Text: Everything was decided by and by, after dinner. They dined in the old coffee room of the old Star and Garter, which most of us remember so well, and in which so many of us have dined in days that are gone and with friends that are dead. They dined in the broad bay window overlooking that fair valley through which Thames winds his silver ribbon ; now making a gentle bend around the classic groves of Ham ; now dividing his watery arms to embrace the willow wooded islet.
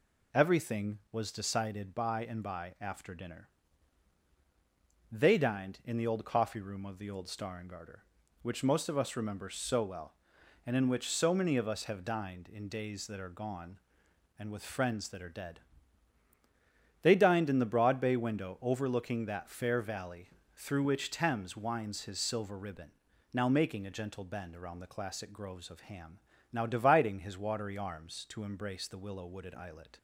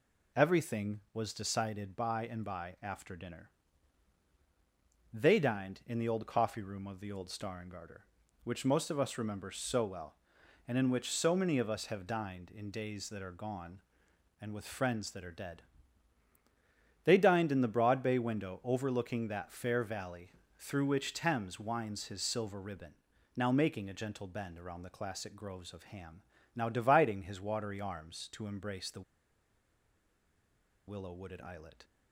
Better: first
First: pauses between "valley" and "through"; slight; at 20.2 s; 0.26 s long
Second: pauses between "valley" and "through"; slight; at 20.3 s; 0.26 s long // pauses between "the" and "willow"; strong; at 29.0 s; 1.8 s long

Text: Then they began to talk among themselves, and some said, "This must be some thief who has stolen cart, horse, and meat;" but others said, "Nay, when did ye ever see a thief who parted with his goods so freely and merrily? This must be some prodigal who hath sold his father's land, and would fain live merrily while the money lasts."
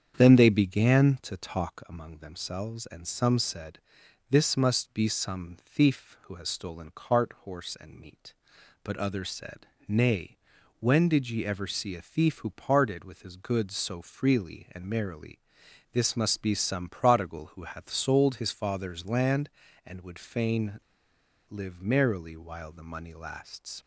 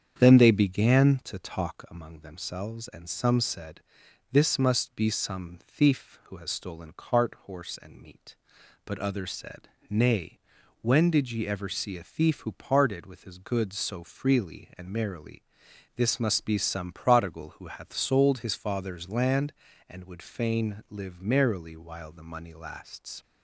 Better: second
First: starts louder than the rest; strong; until 1.1 s; 8 dB // pauses between "fain" and "live"; noticeable; at 20.7 s; 0.71 s long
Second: starts louder than the rest; strong; until 1.1 s; 8 dB

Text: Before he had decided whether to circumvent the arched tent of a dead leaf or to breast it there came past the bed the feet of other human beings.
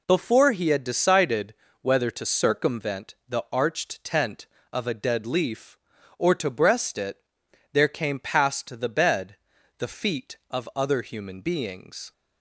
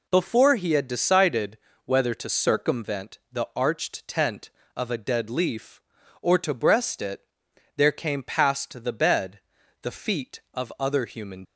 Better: first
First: pauses between "decided" and "whether"; slight; at 1.5 s; 0.26 s long // pauses between "it" and "there"; noticeable; at 7.1 s; 0.54 s long // pauses between "bed" and "the"; at 9.3 s; 0.42 s long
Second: pauses between "decided" and "whether"; slight; at 1.5 s; 0.26 s long // pauses between "it" and "there"; noticeable; at 7.2 s; 0.54 s long // pauses between "bed" and "the"; at 9.3 s; 0.42 s long // stops before "beings"; at 11.4 s

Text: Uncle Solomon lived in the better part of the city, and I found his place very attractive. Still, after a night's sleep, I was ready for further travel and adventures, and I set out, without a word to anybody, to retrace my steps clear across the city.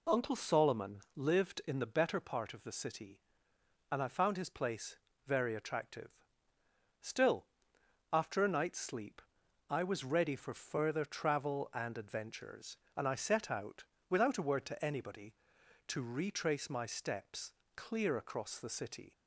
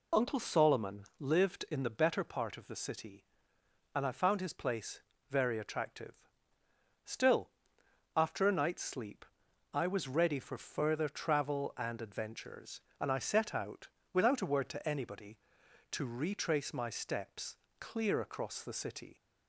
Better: first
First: pauses between "Solomon" and "lived"; slight; at 0.9 s; 0.16 s long // pauses between "place" and "very"; slight; at 4.9 s; 0.30 s long // pauses between "steps" and "clear"; slight; at 17.5 s; 0.24 s long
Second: loses the start of "Uncle"; at 0.1 s; 25 ms // pauses between "Solomon" and "lived"; slight; at 1.0 s; 0.16 s long // pauses between "place" and "very"; slight; at 4.9 s; 0.30 s long // pauses between "steps" and "clear"; slight; at 17.5 s; 0.24 s long

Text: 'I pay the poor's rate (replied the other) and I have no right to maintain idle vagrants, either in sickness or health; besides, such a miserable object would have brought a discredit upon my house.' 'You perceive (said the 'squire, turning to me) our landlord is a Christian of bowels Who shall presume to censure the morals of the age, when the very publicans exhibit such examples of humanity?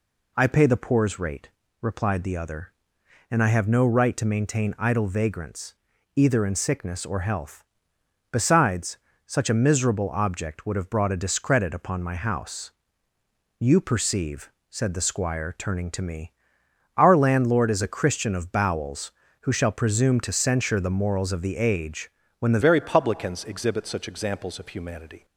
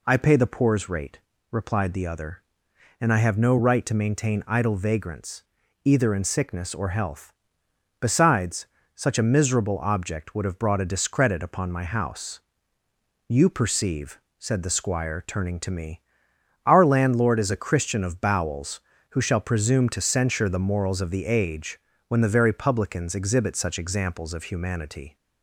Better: second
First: changes voice at "very"; from 22.6 s on; 2.6 s long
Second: none

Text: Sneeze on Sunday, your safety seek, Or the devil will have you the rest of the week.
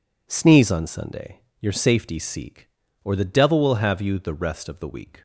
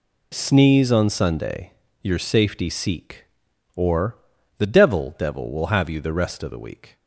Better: first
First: none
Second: pauses between "Or" and "the"; at 4.1 s; 0.40 s long // says "devil" twice; at 5.1 s

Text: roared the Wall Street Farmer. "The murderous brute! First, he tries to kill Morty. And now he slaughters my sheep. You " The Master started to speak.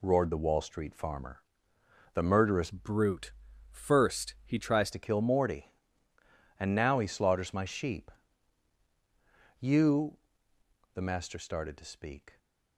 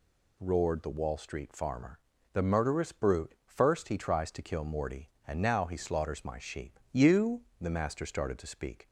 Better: second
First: changes voice from "brute" to "tries"; from 2.7 to 4.8 s; 2.1 s long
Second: none

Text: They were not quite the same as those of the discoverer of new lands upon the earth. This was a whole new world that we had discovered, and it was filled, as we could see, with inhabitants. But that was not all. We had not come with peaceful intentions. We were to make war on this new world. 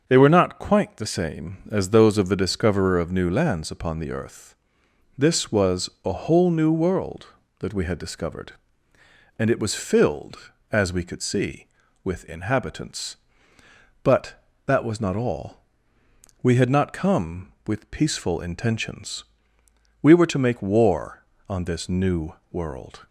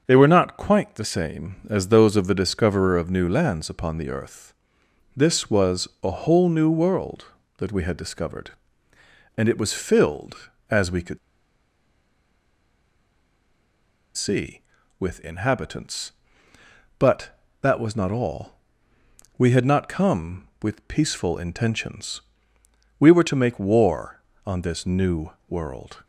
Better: first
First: starts louder than the rest; until 1.0 s; 6.5 dB // pauses between "new" and "world"; slight; at 22.3 s; 0.18 s long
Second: starts louder than the rest; until 1.0 s; 6.5 dB // pauses between "could" and "see"; strong; at 11.1 s; 2.9 s long // pauses between "new" and "world"; slight; at 25.2 s; 0.18 s long

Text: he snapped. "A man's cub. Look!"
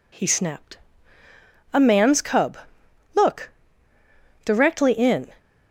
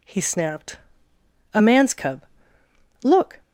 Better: second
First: goes on to say "Directly in"; noticeable; from 4.4 s on; 0.84 s long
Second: none

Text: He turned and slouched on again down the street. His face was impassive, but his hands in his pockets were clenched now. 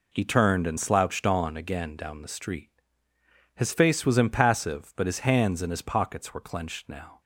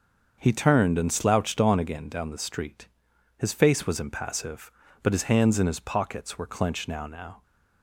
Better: first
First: none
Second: starts louder than the rest; until 1.4 s; 6.5 dB // says "now" twice; at 7.0 s

